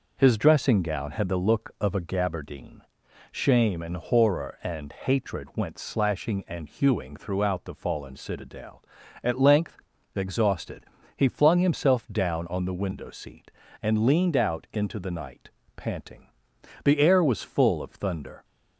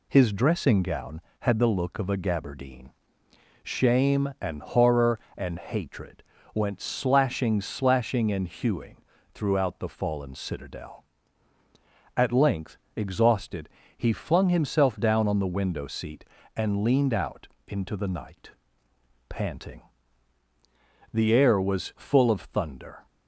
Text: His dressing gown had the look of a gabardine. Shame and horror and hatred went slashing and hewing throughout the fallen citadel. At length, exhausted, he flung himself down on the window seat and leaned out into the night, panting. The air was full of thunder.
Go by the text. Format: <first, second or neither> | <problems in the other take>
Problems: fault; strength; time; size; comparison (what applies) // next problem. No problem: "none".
first | pauses between "hatred" and "went"; slight; at 6.2 s; 0.32 s long // says "slashing" twice; at 7.6 s // pauses between "hewing" and "throughout"; at 8.9 s; 0.38 s long // pauses between "out" and "into"; slight; at 17.4 s; 0.20 s long